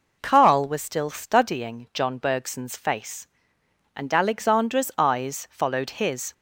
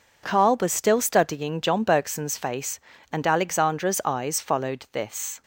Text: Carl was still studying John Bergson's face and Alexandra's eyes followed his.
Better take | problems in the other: first | says "this" for "his"; at 4.9 s

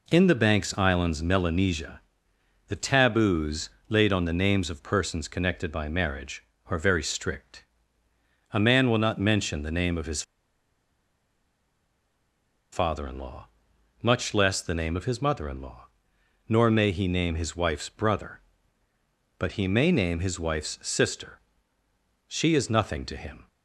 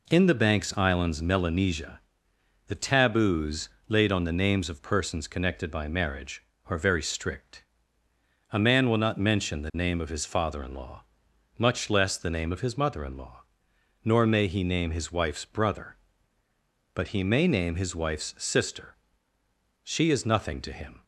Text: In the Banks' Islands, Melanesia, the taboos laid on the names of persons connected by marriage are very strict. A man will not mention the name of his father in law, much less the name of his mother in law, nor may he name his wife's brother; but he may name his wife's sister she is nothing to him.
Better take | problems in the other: second | pauses between "taboos" and "laid"; slight; at 3.6 s; 0.18 s long; slight in the second // pauses between "his" and "father"; strong; at 10.2 s; 2.5 s long // pauses between "sister" and "she"; noticeable; at 21.3 s; 0.88 s long; noticeable in the second

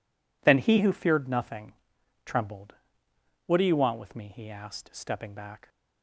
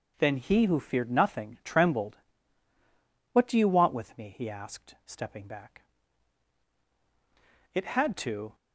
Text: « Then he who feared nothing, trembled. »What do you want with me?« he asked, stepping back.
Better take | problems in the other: first | goes on to say "It had to"; noticeable; from 7.7 s on; 0.82 s long

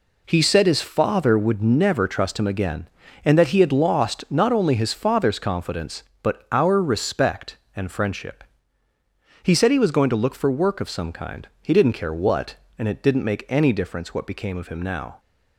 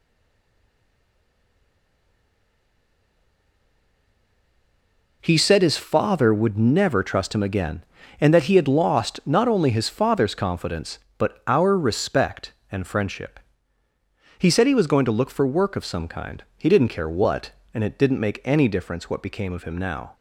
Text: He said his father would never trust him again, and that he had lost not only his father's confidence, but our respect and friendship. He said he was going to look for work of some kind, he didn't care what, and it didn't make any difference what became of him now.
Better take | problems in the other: first | stays silent before the first word; strong; until 5.2 s; 5.2 s long

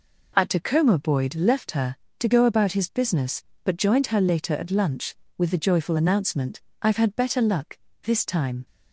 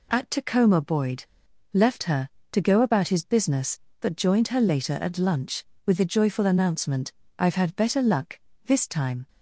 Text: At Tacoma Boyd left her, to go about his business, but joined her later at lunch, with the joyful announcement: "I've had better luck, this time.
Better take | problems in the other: first | pauses between "Boyd" and "left"; at 1.2 s; 0.45 s long

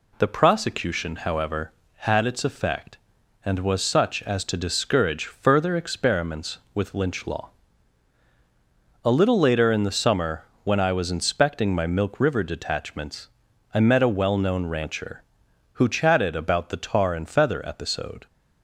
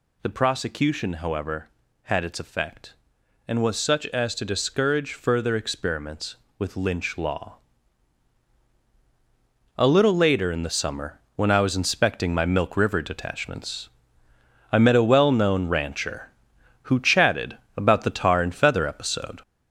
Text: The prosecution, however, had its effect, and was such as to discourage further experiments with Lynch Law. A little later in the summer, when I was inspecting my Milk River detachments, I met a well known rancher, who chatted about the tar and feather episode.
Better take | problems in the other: first | gets louder; noticeable; throughout; 5.5 dB // pauses between "chatted" and "about"; slight; at 17.5 s; 0.22 s long

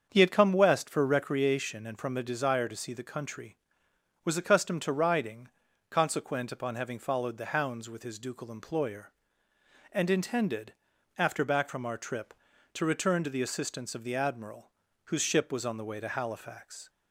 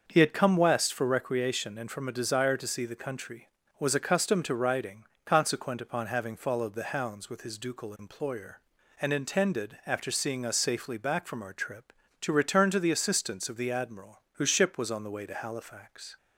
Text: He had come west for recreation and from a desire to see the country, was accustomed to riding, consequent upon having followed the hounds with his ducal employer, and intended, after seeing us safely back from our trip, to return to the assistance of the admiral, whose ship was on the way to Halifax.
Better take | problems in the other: second | starts louder than the rest; strong; until 1.1 s; 7 dB; also in the second // skips "seeing us safely"; at 11.4 s

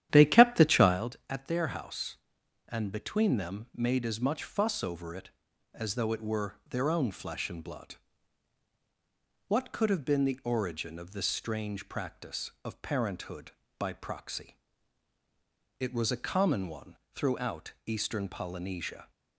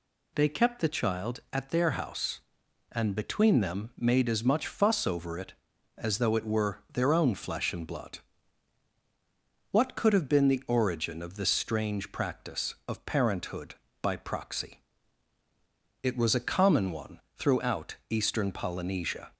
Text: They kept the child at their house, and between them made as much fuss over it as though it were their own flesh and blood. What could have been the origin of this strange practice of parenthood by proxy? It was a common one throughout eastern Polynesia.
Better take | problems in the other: second | starts louder than the rest; strong; until 1.1 s; 11 dB // pauses between "one" and "throughout"; slight; at 16.9 s; 0.18 s long; slight in the second

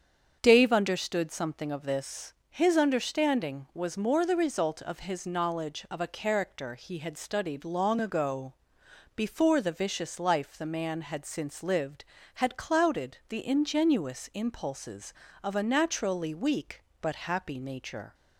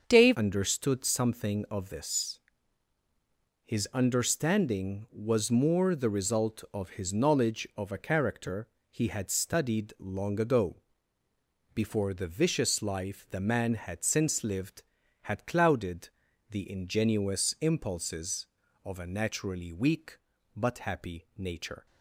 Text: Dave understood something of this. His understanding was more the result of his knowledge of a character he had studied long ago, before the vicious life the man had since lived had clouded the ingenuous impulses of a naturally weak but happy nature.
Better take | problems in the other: first | starts louder than the rest; until 1.0 s; 6.5 dB; strong in the first // changes voice at "understood"; from 0.3 s on; 21.5 s long // pauses between "character" and "he"; slight; at 8.6 s; 0.22 s long // pauses between "clouded" and "the"; at 16.0 s; 0.40 s long

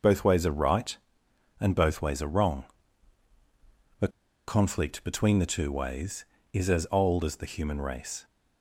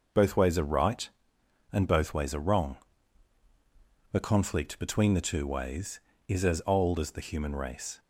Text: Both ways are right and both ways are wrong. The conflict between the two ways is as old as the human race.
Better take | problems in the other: second | pauses between "The" and "conflict"; at 4.0 s; 0.39 s long

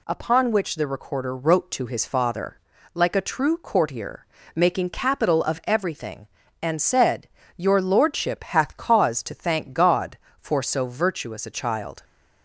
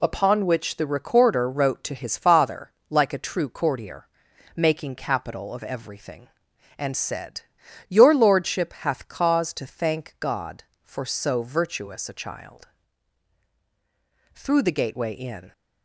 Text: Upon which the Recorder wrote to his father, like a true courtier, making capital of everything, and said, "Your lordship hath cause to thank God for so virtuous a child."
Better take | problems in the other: first | goes on to say "Through the gateway in"; noticeable; from 14.3 s on; 1.2 s long

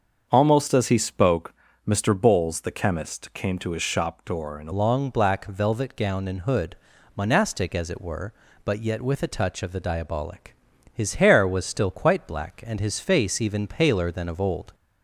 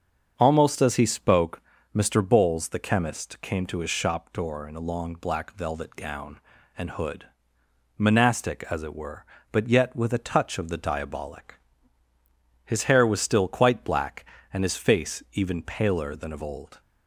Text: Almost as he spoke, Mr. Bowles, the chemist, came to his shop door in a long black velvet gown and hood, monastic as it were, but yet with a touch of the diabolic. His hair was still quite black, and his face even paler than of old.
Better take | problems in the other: second | starts louder than the rest; until 1.3 s; 7 dB; also in the second // changes voice at "long"; from 4.7 s on; 10.0 s long

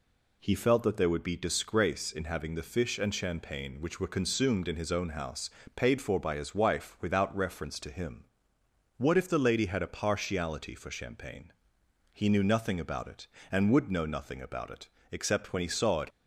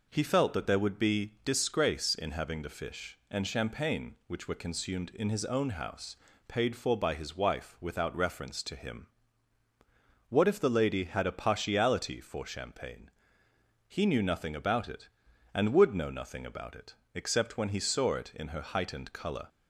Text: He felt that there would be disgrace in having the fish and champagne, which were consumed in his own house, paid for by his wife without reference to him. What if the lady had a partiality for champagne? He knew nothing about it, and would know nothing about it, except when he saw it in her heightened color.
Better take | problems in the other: second | stops before "in her heightened color"; at 16.1 s

